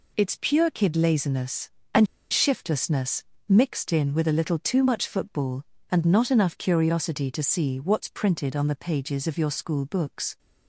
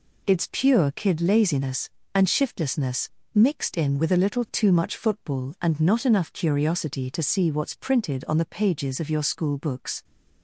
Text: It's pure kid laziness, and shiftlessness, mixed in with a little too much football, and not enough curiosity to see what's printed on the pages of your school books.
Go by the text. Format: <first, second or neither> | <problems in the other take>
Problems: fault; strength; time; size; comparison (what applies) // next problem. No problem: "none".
second | pauses between "and" and "shiftlessness"; slight; at 2.0 s; 0.25 s long